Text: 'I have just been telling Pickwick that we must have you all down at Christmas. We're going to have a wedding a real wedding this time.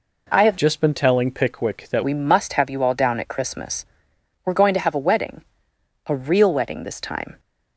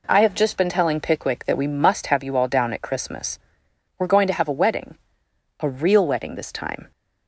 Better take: second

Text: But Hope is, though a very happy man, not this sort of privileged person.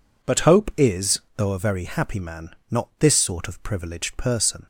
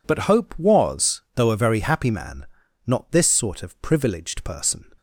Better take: first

